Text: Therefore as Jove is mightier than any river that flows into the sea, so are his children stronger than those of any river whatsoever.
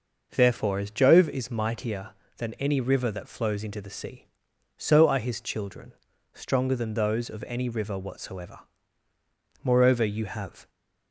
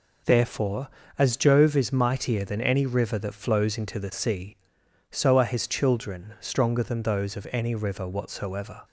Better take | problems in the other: second | pauses between "children" and "stronger"; at 5.9 s; 0.40 s long // goes on to say "Moreover you have"; noticeable; from 9.6 s on; 1.0 s long

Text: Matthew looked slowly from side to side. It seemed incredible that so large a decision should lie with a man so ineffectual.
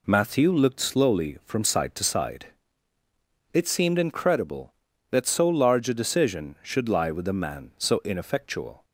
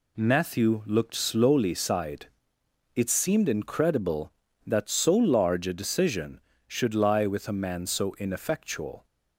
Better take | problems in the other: first | skips "from side to"; at 1.7 s

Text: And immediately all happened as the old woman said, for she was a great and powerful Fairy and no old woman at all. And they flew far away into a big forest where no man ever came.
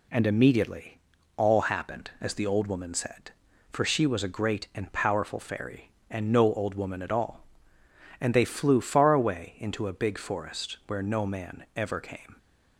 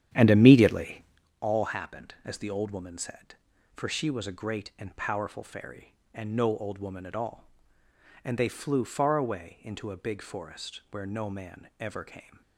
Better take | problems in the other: first | starts louder than the rest; strong; until 1.3 s; 10 dB // pauses between "immediately" and "all"; at 1.0 s; 0.38 s long; also in the first

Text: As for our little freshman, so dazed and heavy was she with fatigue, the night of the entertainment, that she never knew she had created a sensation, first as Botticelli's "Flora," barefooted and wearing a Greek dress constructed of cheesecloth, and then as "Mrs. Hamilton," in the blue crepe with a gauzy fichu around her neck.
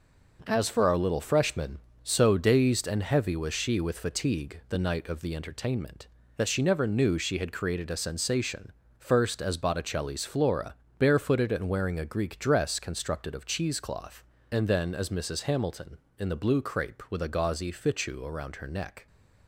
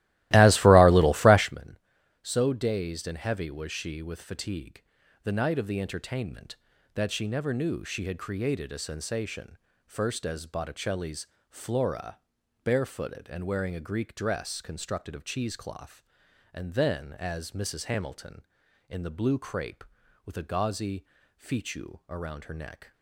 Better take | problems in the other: first | starts louder than the rest; strong; until 1.5 s; 17 dB // pauses between "Botticelli's" and "Flora"; slight; at 11.2 s; 0.24 s long // pauses between "gauzy" and "fichu"; slight; at 21.0 s; 0.32 s long

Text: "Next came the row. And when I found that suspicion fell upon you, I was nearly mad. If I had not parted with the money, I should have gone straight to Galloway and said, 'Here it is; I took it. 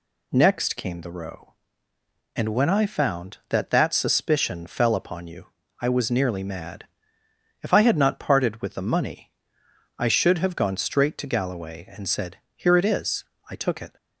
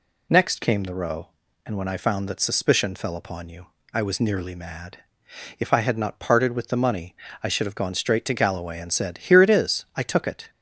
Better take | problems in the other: second | says "that" twice; at 3.7 s

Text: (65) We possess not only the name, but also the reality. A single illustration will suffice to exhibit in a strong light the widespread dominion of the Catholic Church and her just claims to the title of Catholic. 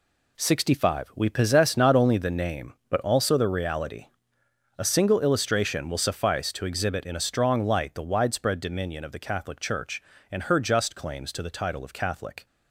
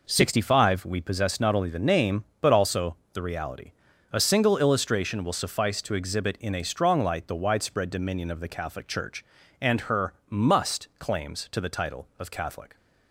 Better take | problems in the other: first | pauses between "also" and "the"; slight; at 2.9 s; 0.18 s long // says "must" for "just"; at 10.2 s

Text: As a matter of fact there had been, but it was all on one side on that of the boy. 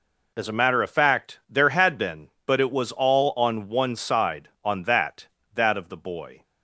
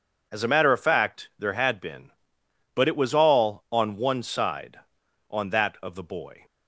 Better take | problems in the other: second | says "that" twice; at 5.5 s

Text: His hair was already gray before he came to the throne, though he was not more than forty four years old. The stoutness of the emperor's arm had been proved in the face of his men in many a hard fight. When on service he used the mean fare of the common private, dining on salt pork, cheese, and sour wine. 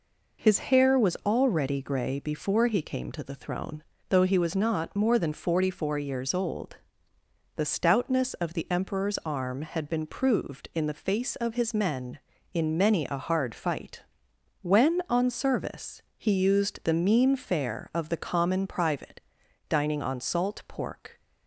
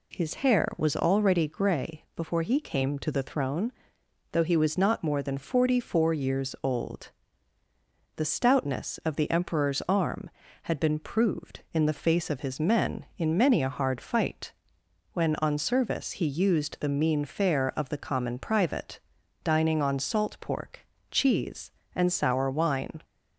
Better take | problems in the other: second | pauses between "service" and "he"; slight; at 15.9 s; 0.16 s long // stops before "cheese and sour wine"; at 21.1 s

